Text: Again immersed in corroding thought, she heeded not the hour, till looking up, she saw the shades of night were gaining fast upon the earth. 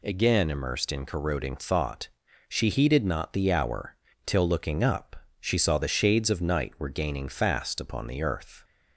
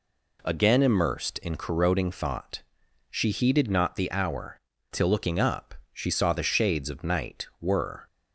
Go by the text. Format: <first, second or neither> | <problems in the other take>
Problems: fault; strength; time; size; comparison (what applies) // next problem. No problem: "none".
first | stops before "gaining fast upon the earth"; at 8.0 s